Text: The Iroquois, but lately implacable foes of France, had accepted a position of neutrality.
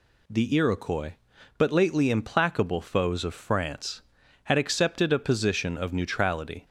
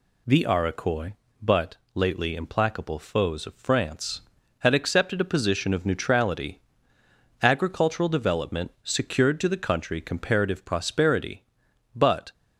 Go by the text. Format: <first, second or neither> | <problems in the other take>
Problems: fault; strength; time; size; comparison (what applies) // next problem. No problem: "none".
first | pauses between "but" and "lately"; slight; at 1.7 s; 0.18 s long // goes on to say "Agricultural development secured to the country comparative prosperity but"; strong; from 7.4 s on; 4.9 s long